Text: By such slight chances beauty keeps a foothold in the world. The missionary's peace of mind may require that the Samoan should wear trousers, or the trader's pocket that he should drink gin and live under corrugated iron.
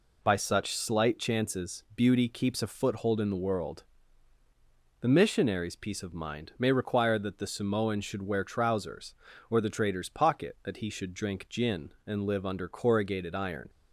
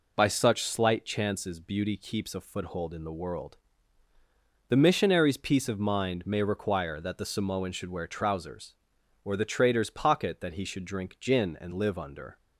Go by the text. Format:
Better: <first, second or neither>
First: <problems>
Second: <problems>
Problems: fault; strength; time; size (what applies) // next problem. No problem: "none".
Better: first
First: none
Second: stops before "corrugated iron"; at 12.3 s